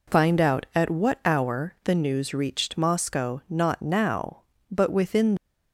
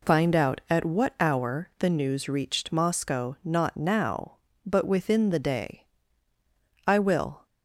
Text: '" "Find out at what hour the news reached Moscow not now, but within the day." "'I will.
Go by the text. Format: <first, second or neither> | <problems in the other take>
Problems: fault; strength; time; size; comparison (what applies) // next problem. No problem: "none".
second | stops before "the day I will"; at 5.3 s